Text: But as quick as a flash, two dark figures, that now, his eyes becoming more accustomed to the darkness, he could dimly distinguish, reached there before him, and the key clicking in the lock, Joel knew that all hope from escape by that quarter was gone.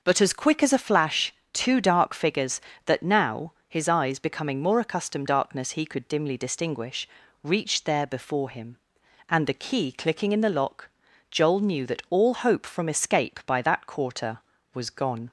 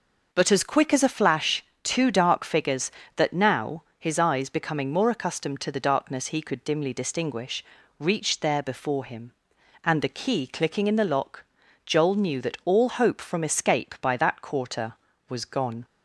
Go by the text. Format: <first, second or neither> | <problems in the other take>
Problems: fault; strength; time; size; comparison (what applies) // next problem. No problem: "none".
second | skips "to the"; at 5.2 s